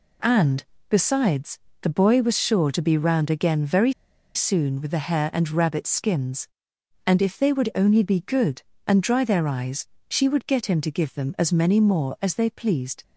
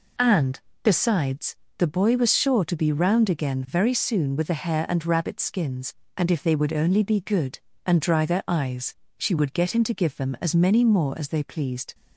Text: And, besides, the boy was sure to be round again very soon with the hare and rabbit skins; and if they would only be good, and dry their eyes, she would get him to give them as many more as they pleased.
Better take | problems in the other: second | pauses between "very" and "soon"; at 3.9 s; 0.42 s long

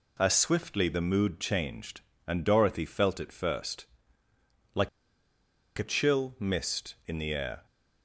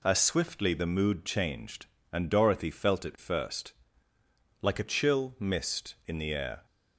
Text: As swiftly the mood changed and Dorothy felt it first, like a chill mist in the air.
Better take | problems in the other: second | pauses between "like" and "a"; noticeable; at 4.8 s; 0.90 s long

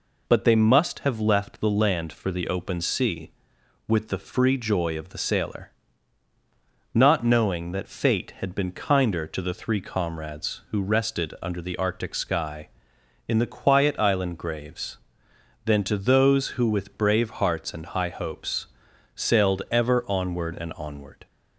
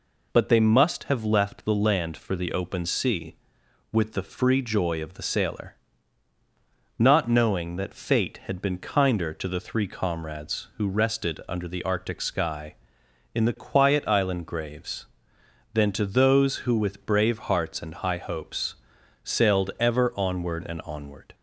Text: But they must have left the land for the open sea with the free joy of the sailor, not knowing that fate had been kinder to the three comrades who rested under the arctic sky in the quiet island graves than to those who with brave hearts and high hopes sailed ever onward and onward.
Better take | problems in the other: neither | pauses between "hopes" and "sailed"; noticeable; the same in both

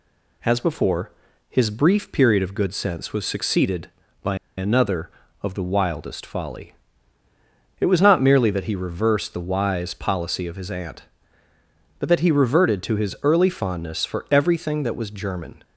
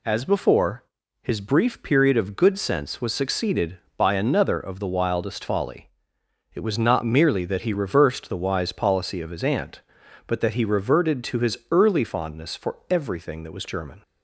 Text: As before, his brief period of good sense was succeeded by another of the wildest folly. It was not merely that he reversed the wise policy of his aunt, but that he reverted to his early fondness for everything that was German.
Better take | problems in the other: second | pauses between "by" and "another"; slight; at 4.3 s; 0.20 s long

